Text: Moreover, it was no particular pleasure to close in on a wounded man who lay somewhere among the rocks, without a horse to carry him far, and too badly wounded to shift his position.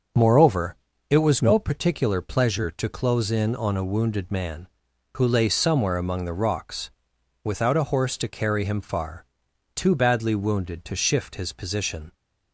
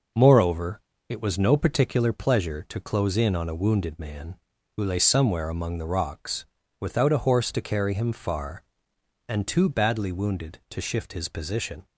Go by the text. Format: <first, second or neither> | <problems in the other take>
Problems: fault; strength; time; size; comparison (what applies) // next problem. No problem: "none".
second | starts louder than the rest; until 1.4 s; 6.5 dB // skips "and"; at 9.4 s